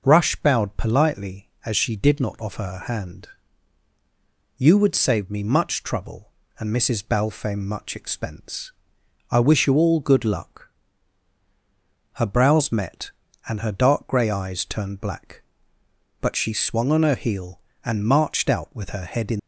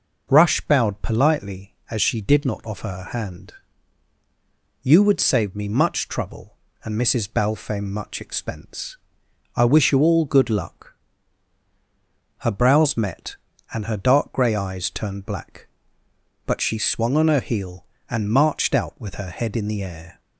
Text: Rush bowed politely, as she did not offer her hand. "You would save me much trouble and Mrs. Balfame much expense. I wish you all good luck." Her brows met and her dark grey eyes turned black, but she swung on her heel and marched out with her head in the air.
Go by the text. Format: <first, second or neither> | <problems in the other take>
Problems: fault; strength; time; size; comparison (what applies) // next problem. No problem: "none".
second | stops before "the air"; at 19.3 s